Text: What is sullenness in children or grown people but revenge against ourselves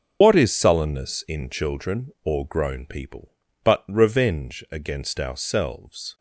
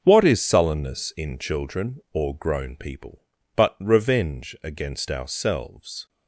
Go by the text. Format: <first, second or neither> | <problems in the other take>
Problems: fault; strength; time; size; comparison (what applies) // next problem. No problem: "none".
second | loses the start of "What"; at 0.2 s; 65 ms // starts louder than the rest; until 1.2 s; 7 dB; also in the second